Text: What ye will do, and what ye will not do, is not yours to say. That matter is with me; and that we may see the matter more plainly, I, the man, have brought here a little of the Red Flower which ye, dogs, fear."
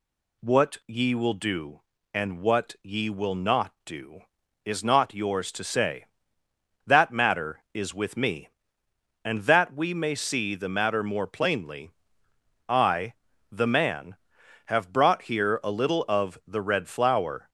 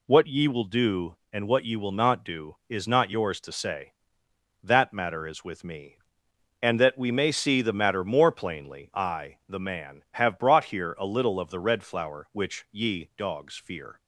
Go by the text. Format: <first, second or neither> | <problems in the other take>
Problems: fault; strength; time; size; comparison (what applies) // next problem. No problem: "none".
second | stops before "which ye dogs fear"; at 17.4 s